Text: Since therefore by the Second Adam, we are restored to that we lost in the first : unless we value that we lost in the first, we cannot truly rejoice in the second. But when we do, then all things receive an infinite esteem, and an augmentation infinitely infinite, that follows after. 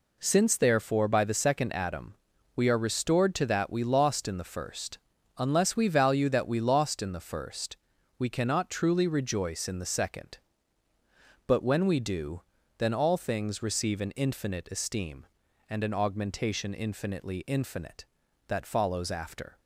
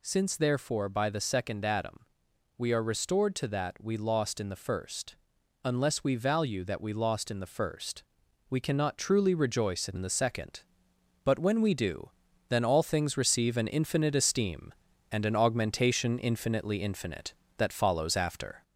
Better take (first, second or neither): first